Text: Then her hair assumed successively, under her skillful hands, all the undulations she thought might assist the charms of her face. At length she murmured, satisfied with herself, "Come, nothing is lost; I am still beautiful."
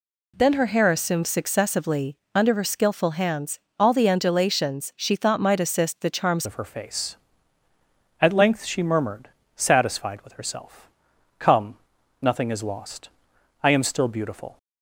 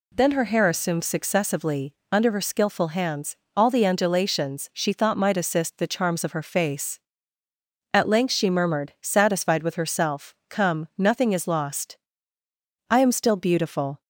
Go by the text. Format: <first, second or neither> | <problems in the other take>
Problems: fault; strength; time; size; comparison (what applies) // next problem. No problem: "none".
second | changes voice at "of"; from 6.4 s on; 8.1 s long